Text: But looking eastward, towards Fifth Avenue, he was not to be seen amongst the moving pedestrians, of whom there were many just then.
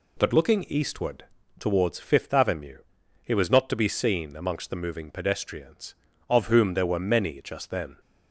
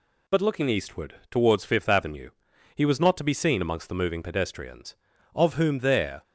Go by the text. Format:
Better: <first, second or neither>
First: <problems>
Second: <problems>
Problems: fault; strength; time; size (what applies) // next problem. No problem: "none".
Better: first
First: none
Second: stops before "were many just then"; at 6.2 s